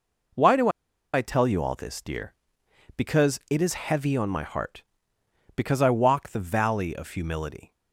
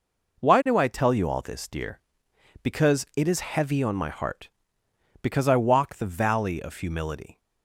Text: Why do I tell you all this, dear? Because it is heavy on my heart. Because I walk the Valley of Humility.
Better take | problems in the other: second | pauses between "do" and "I"; at 0.6 s; 0.44 s long

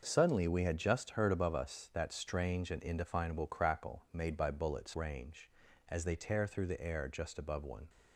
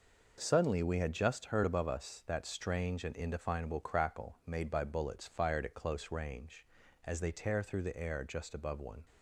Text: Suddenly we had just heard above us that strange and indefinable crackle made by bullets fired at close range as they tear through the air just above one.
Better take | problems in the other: second | skips "fired at close"; at 4.9 s

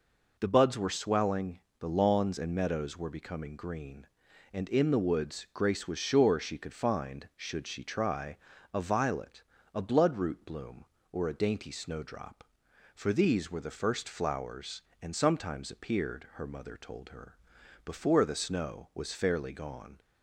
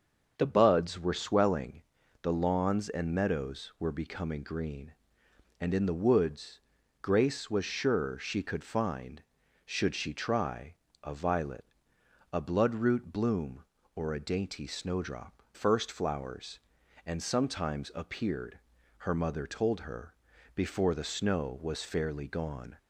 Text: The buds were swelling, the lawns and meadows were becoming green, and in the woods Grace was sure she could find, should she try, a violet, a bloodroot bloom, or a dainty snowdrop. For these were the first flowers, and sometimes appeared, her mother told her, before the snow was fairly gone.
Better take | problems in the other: first | starts louder than the rest; until 1.3 s; 6.5 dB // pauses between "woods" and "Grace"; at 6.5 s; 0.42 s long // skips "For these were the"; at 15.4 s

